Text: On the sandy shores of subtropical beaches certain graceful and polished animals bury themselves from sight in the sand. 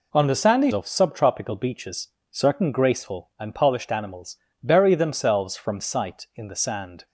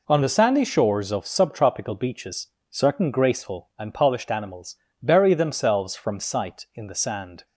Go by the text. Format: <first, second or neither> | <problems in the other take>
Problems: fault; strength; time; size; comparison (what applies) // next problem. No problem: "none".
second | skips "shores"; at 0.7 s // pauses between "beaches" and "certain"; slight; at 2.0 s; 0.22 s long; slight in the second // pauses between "animals" and "bury"; slight; at 4.3 s; 0.26 s long; slight in the second